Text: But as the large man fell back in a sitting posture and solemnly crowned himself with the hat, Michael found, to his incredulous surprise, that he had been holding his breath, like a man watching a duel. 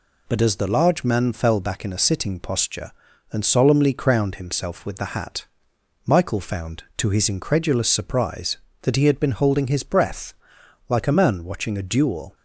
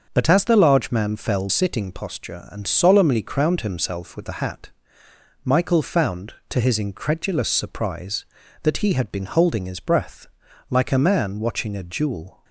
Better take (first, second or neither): first